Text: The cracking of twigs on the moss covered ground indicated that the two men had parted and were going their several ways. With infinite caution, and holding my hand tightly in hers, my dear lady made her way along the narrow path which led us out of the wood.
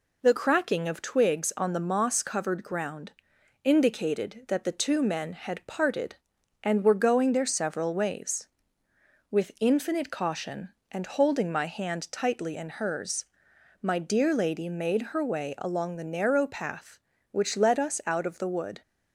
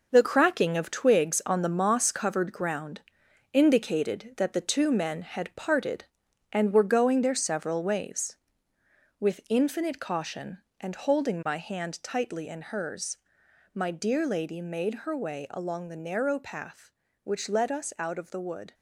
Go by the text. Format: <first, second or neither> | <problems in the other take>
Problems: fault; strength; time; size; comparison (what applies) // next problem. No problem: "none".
first | gets quieter; strong; throughout; 7.5 dB // pauses between "ground" and "indicated"; noticeable; at 3.0 s; 0.50 s long; noticeable in the first